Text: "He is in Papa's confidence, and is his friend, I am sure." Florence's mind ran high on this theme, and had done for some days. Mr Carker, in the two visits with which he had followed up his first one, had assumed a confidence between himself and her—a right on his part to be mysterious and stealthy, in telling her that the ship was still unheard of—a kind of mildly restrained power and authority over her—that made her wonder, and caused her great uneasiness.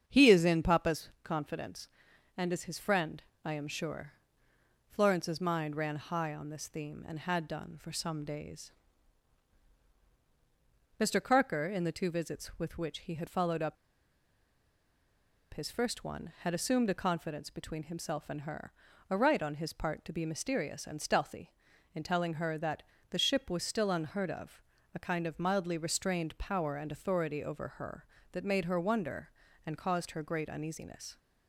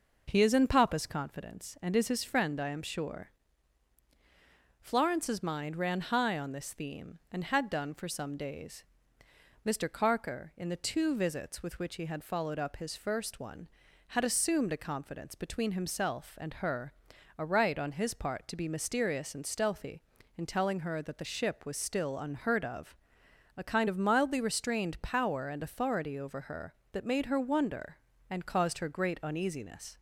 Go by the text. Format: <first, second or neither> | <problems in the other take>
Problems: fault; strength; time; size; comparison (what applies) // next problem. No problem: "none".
second | starts louder than the rest; strong; until 1.0 s; 7.5 dB // pauses between "up" and "his"; strong; at 13.7 s; 1.7 s long // pauses between "that" and "the"; slight; at 22.8 s; 0.26 s long